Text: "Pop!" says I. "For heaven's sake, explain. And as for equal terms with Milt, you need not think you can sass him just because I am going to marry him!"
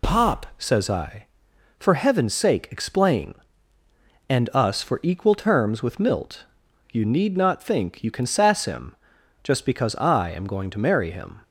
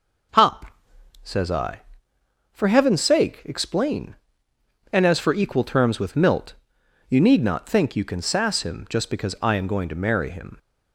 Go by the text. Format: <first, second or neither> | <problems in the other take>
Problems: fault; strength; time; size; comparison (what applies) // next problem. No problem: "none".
second | says "us" for "as"; at 4.5 s // pauses between "him" and "just"; noticeable; at 8.9 s; 0.48 s long